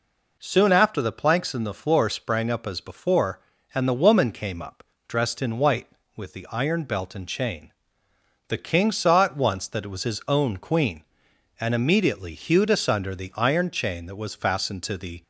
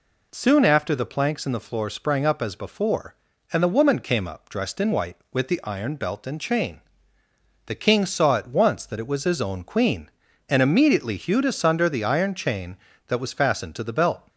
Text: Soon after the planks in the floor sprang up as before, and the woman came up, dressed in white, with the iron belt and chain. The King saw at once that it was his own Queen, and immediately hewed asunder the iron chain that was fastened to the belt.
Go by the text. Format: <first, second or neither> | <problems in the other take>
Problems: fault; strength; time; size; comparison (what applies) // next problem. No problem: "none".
second | stops before "belt"; at 15.2 s